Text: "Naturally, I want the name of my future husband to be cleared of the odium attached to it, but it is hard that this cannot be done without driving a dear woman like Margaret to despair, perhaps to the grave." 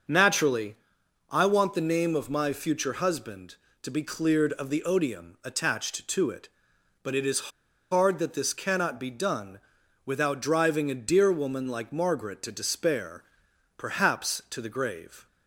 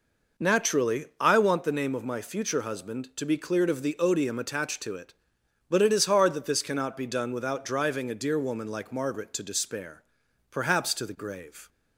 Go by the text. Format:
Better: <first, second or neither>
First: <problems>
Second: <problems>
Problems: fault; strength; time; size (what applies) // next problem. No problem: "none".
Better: second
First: starts louder than the rest; until 1.6 s; 6.5 dB // pauses between "is" and "hard"; at 7.5 s; 0.40 s long // pauses between "done" and "without"; noticeable; at 9.5 s; 0.46 s long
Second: none